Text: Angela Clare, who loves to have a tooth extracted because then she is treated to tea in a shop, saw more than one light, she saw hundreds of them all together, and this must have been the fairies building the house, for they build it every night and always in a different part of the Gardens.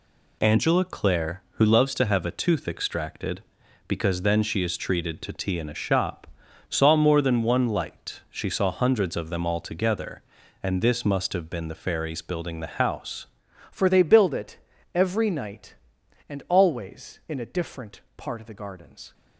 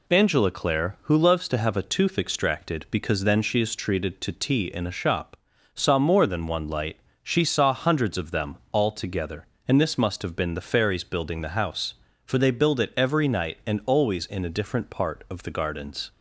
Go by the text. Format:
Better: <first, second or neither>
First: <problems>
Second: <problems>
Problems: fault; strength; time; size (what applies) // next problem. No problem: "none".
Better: second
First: changes voice at "for"; from 13.7 s on; 5.4 s long // pauses between "it" and "every"; slight; at 14.5 s; 0.36 s long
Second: none